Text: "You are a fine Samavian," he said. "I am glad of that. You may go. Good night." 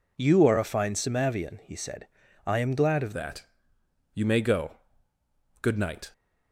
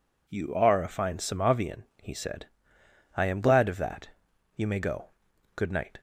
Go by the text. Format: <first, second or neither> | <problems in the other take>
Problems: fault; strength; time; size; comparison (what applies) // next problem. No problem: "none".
second | changes voice at "that"; from 3.1 s on; 3.0 s long